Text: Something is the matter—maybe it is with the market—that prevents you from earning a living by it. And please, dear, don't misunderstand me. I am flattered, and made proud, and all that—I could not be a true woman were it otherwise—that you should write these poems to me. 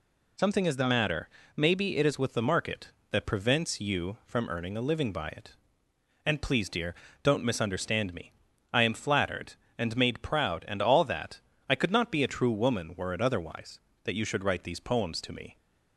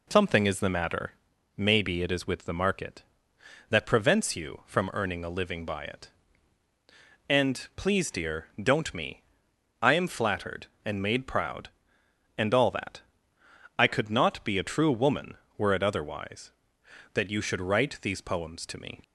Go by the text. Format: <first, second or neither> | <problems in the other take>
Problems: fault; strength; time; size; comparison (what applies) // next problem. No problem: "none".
first | skips "misunderstand"; at 8.9 s